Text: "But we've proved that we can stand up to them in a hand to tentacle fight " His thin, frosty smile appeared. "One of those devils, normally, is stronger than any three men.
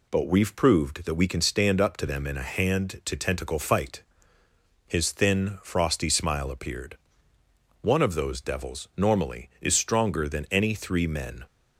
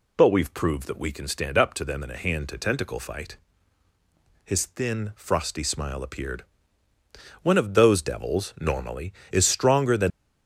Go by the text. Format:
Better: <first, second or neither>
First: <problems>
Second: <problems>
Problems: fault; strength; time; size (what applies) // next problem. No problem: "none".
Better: first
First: none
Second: stops before "any three men"; at 10.1 s